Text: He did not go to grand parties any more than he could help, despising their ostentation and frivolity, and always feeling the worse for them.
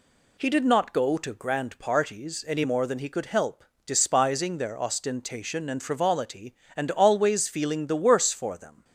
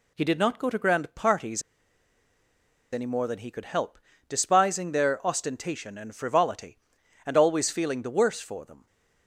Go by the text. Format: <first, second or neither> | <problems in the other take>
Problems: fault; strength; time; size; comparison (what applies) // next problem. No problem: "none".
first | pauses between "parties" and "any"; strong; at 1.6 s; 1.3 s long